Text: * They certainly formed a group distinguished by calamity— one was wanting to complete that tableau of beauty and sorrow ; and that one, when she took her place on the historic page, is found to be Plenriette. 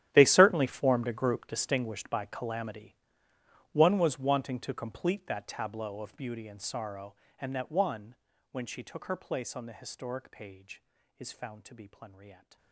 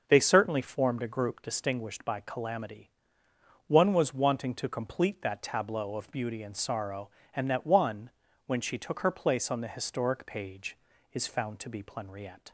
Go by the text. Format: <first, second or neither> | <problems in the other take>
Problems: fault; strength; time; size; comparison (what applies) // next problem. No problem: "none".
second | gets quieter; strong; throughout; 19 dB // starts louder than the rest; strong; until 1.1 s; 11.5 dB; noticeable in the second